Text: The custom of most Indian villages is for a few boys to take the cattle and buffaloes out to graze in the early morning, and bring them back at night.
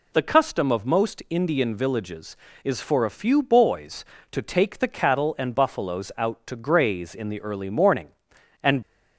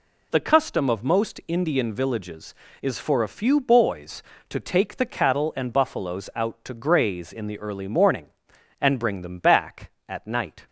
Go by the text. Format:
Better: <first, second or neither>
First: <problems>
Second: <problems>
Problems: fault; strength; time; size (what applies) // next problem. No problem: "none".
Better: second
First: stops before "bring them back at night"; at 8.8 s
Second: none